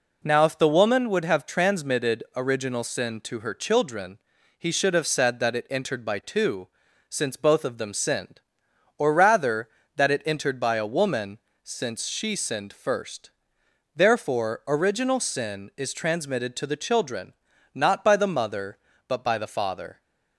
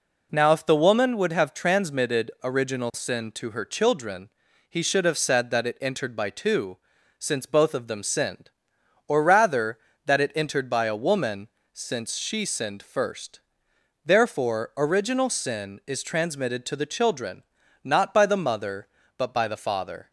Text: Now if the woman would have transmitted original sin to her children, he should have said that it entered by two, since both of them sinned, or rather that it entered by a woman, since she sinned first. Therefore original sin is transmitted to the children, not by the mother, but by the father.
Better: neither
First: none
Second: none

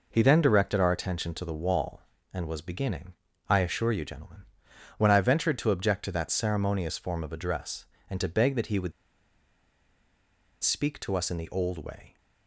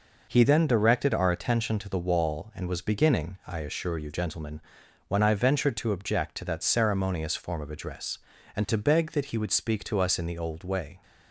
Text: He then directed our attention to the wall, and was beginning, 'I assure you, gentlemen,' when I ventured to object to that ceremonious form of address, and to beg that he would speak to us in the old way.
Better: second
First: pauses between "would" and "speak"; strong; at 8.9 s; 1.7 s long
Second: none

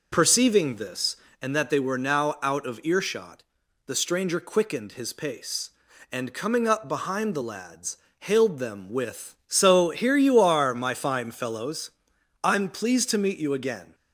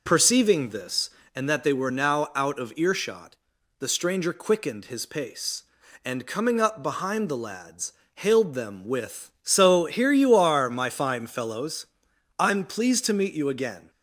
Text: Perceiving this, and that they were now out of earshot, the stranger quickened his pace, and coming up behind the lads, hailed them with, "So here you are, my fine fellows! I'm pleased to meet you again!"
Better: neither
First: none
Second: none

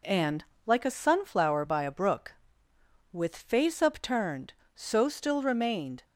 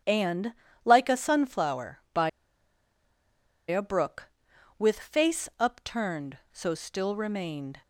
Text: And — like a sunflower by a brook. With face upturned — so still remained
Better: first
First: none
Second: starts louder than the rest; strong; until 1.3 s; 9.5 dB // pauses between "by" and "a"; strong; at 2.2 s; 1.3 s long

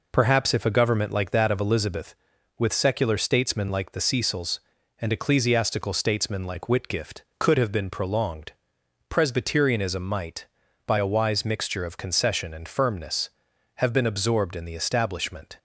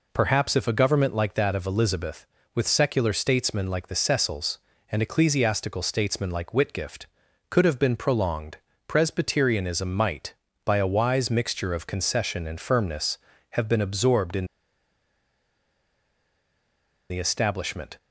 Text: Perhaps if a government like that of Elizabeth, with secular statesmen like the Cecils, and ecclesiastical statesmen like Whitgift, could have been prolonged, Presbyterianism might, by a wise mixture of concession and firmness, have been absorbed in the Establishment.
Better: first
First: none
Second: pauses between "in" and "the"; strong; at 14.4 s; 2.6 s long

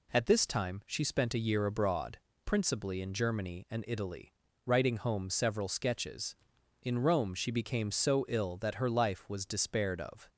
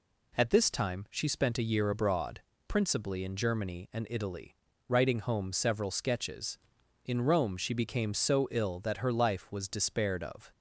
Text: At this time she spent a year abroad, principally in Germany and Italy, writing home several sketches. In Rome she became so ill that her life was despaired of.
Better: neither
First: none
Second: none

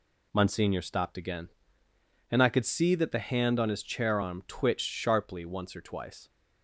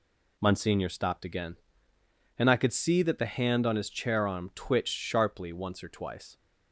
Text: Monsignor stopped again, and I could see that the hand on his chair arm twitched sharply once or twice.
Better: neither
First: none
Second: none

